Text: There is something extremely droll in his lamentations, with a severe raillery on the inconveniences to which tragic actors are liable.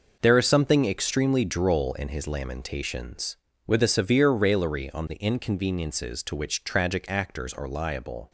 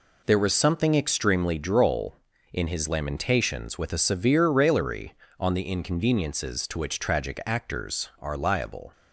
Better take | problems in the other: first | says "was" for "is"; at 0.3 s

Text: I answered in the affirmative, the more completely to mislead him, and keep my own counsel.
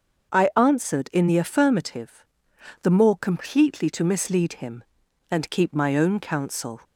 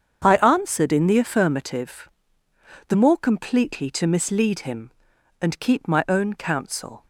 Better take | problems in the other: neither | starts louder than the rest; the same in both

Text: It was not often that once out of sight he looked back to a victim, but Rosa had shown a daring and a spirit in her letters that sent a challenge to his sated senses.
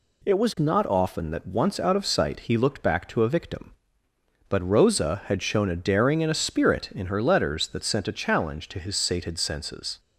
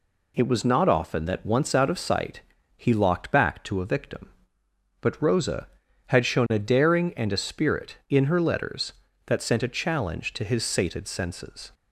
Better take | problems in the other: first | pauses between "sight" and "he"; slight; at 2.4 s; 0.34 s long // says "locked" for "looked"; at 2.9 s

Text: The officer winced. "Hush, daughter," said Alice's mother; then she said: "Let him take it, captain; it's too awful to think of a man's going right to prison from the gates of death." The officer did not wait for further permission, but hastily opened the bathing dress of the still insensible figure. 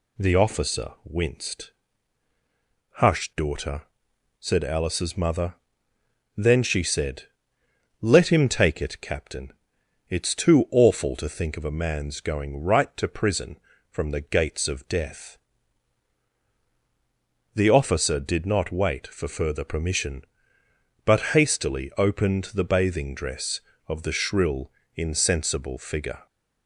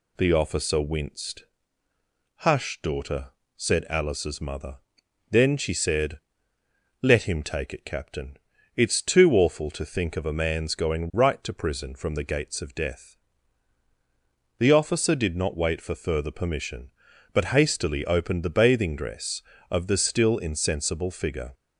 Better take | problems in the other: second | says "shrill" for "still"; at 24.1 s

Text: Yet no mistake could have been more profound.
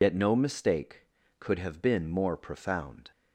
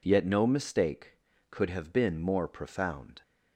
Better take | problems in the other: second | loses the start of "Yet"; at 0.0 s; 95 ms

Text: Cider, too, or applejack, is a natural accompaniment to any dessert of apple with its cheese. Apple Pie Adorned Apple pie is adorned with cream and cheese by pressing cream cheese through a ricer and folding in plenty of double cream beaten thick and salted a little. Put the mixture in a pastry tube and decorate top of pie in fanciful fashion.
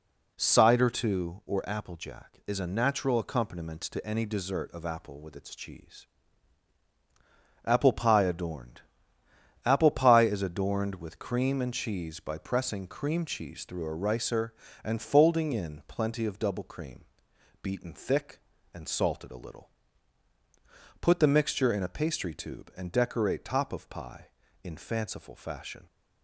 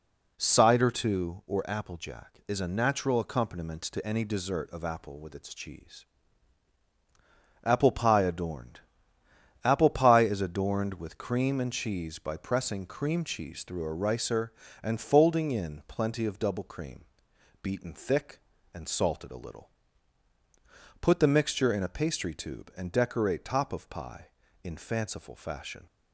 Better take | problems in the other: neither | pauses between "Adorned" and "Apple"; noticeable; the same in both // pauses between "cream" and "beaten"; noticeable; the same in both

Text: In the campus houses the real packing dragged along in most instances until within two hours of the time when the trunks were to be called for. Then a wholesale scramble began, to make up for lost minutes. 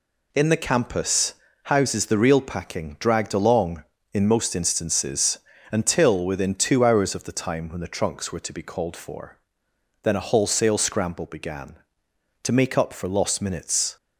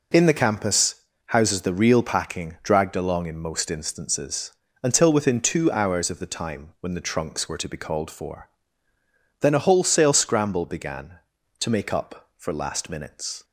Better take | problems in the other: first | pauses between "campus" and "houses"; slight; at 0.9 s; 0.30 s long; slight in the first // pauses between "instances" and "until"; slight; at 4.5 s; 0.32 s long; slight in the first // says "last" for "lost"; at 12.5 s

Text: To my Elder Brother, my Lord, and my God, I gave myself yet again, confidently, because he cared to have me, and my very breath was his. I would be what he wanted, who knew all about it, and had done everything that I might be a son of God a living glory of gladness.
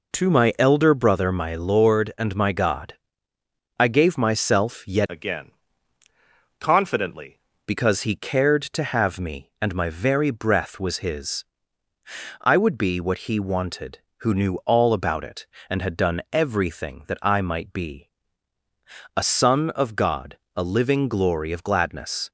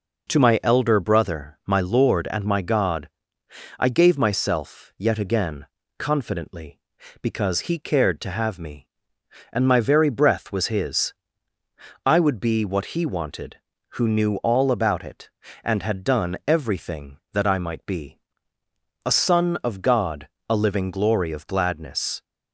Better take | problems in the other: second | changes voice from "again" to "confidently"; from 5.0 to 7.3 s; 2.3 s long // pauses between "be" and "a"; at 18.0 s; 1.0 s long; noticeable in the second // pauses between "God" and "a"; slight; at 20.3 s; 0.18 s long; slight in the second

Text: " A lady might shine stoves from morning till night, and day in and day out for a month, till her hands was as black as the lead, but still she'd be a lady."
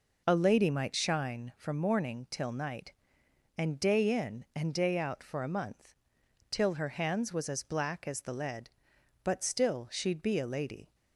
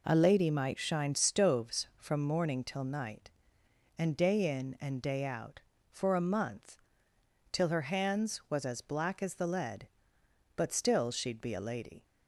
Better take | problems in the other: second | skips "stoves"; at 1.5 s

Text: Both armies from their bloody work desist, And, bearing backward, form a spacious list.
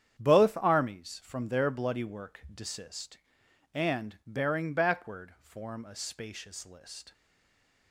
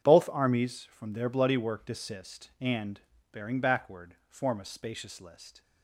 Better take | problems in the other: second | starts louder than the rest; strong; until 1.2 s; 9 dB // stays silent after the last word; slight; from 7.1 s on; 0.8 s long

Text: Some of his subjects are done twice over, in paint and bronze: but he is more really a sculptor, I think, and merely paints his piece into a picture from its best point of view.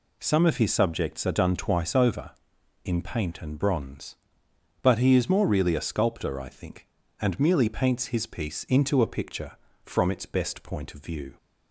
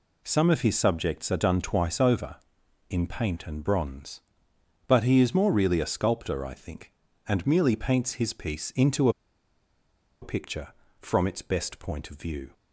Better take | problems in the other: first | pauses between "into" and "a"; at 9.0 s; 1.1 s long

